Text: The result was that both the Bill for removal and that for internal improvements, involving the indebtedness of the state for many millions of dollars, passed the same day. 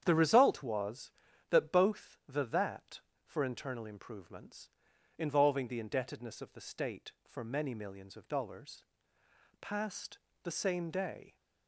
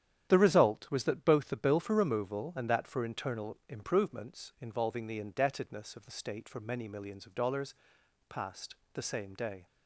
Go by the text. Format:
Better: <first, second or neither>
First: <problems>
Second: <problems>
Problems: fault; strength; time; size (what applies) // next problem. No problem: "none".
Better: second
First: starts louder than the rest; strong; until 1.0 s; 9 dB // skips "Bill for removal and"; at 2.4 s // pauses between "passed" and "the"; slight; at 10.1 s; 0.26 s long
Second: starts louder than the rest; strong; until 1.3 s; 9.5 dB // pauses between "passed" and "the"; slight; at 8.7 s; 0.20 s long